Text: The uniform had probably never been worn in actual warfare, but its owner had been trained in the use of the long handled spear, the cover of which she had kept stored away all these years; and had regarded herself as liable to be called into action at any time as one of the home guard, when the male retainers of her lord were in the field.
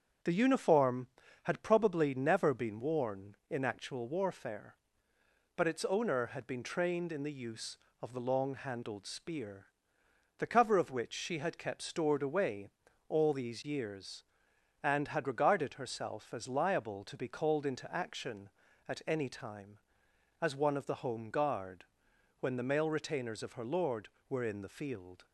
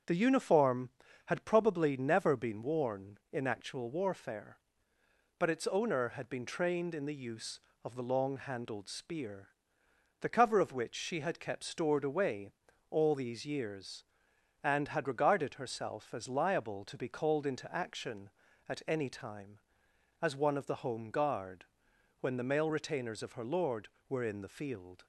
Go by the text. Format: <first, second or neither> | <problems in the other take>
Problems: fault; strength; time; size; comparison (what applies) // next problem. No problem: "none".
neither | starts louder than the rest; strong; the same in both // pauses between "away" and "all"; the same in both